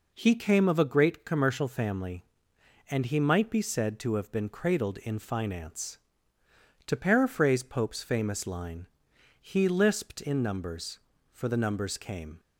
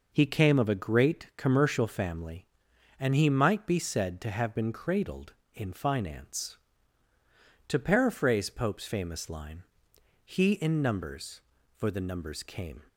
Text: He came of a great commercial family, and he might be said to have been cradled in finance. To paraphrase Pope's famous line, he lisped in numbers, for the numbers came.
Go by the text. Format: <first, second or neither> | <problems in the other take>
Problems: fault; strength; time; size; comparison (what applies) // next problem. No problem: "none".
first | skips "lisped"; at 10.5 s